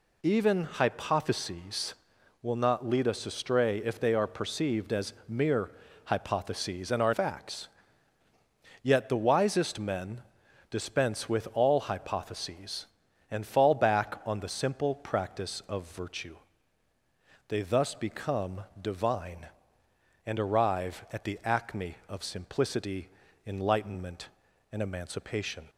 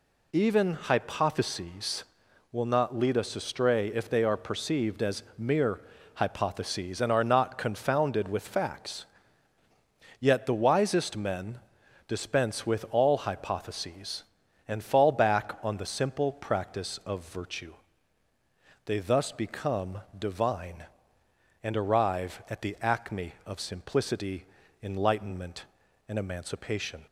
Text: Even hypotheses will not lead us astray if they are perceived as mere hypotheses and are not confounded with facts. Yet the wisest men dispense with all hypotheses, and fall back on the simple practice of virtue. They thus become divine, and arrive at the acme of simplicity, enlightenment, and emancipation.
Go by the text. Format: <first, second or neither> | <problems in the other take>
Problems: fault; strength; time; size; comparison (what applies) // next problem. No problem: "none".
second | pauses between "mere" and "hypotheses"; slight; at 5.7 s; 0.34 s long; slight in the second // skips "not confounded with"; at 7.1 s // pauses between "men" and "dispense"; noticeable; at 10.2 s; 0.48 s long; noticeable in the second // pauses between "become" and "divine"; slight; at 18.6 s; 0.18 s long; slight in the second